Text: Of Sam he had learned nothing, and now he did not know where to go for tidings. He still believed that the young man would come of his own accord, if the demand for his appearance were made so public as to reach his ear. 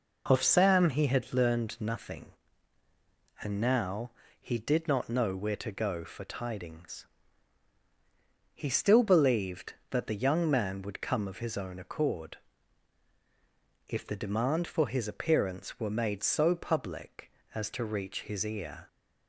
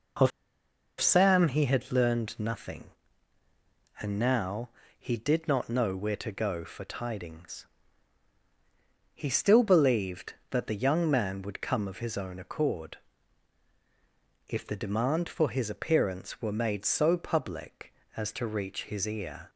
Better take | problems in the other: first | pauses between "Of" and "Sam"; noticeable; at 0.3 s; 0.70 s long // pauses between "now" and "he"; slight; at 4.6 s; 0.30 s long; slight in the first

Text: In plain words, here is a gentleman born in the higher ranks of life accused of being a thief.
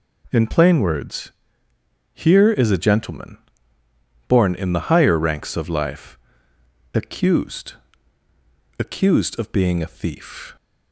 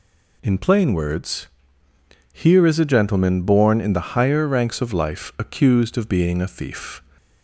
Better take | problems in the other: second | pauses between "gentleman" and "born"; noticeable; at 3.3 s; 0.90 s long // pauses between "life" and "accused"; noticeable; at 6.1 s; 0.78 s long // says "accused" twice; at 8.7 s

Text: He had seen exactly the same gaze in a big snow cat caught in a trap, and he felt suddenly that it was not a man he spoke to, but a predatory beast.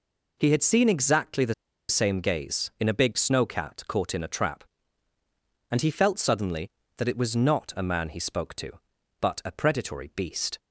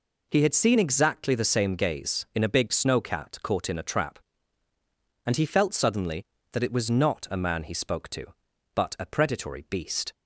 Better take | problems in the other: second | pauses between "the" and "same"; at 1.5 s; 0.36 s long

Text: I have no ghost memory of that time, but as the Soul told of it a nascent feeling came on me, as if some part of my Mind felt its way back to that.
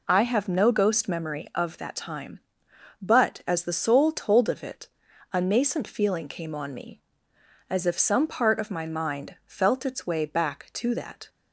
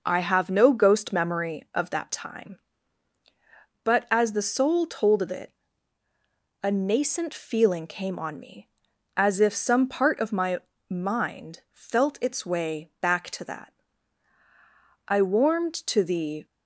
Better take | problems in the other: first | pauses between "it" and "a"; at 5.5 s; 1.1 s long; also in the first // pauses between "my" and "Mind"; slight; at 10.5 s; 0.32 s long // goes on to say "I warmed to the"; from 15.0 s on; 1.3 s long

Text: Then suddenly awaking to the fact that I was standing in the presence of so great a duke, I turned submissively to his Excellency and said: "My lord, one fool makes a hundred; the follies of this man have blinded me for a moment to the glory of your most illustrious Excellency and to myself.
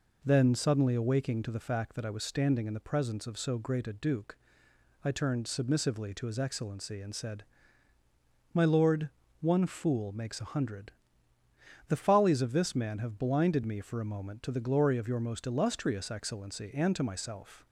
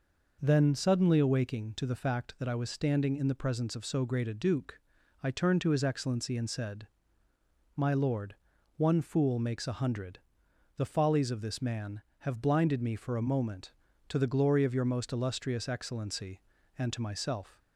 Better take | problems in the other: first | skips "submissively"; at 5.6 s

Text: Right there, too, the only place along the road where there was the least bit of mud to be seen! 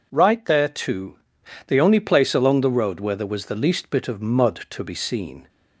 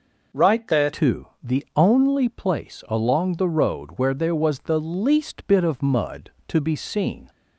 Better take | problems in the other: first | changes voice at "too"; from 0.9 s on; 6.3 s long

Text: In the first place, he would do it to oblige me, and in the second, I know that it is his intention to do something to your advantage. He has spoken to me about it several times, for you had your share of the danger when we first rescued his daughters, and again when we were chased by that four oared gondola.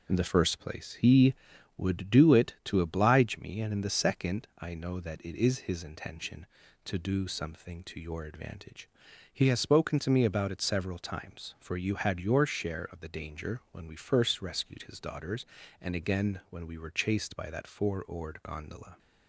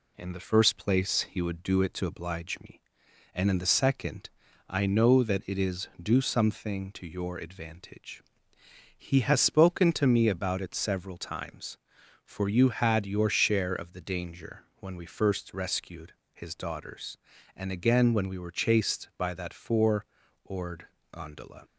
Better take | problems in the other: first | skips "his intention to"; at 5.9 s // pauses between "rescued" and "his"; slight; at 16.1 s; 0.20 s long // pauses between "four" and "oared"; at 20.0 s; 0.40 s long // pauses between "oared" and "gondola"; slight; at 20.8 s; 0.24 s long

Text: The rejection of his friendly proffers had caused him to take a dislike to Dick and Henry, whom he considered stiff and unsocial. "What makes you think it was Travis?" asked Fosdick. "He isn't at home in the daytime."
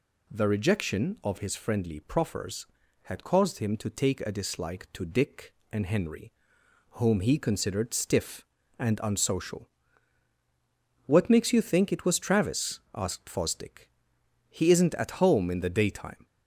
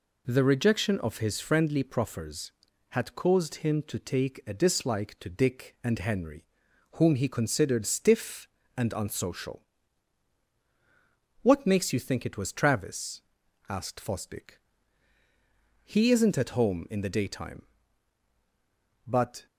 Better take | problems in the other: first | goes on to say "But"; slight; from 19.0 s on; 0.40 s long

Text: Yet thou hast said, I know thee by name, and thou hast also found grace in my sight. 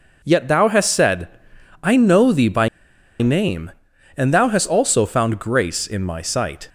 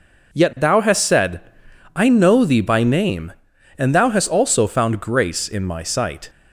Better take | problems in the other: second | pauses between "by" and "name"; noticeable; at 2.6 s; 0.53 s long

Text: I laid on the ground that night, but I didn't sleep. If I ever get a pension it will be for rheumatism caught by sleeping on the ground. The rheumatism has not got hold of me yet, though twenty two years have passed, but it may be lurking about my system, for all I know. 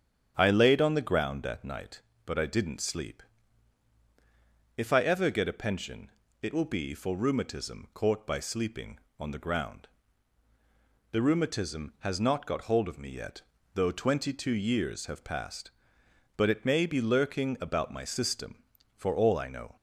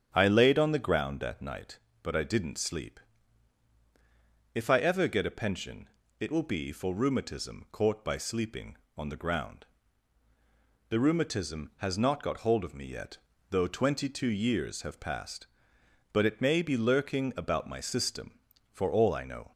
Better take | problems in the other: neither | starts louder than the rest; strong; the same in both // pauses between "pension" and "it"; slight; the same in both

